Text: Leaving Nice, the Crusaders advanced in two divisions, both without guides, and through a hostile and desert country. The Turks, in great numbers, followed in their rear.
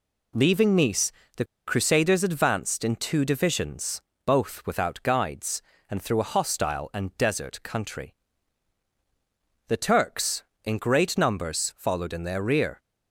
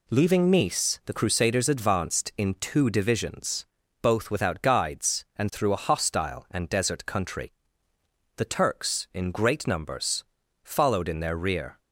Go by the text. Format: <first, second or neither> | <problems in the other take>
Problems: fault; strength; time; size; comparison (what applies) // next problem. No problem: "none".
second | pauses between "the" and "Crusaders"; slight; at 1.4 s; 0.22 s long